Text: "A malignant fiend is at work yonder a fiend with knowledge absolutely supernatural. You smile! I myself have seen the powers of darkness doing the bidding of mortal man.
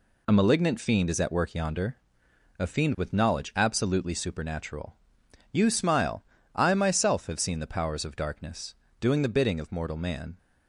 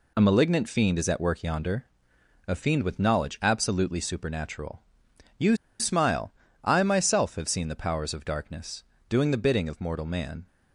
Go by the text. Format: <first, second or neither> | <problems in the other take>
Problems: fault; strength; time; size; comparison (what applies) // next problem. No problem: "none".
first | pauses between "yonder" and "a"; noticeable; at 1.8 s; 0.62 s long; noticeable in the first // pauses between "You" and "smile"; slight; at 5.5 s; 0.24 s long // pauses between "darkness" and "doing"; slight; at 8.8 s; 0.24 s long; slight in the first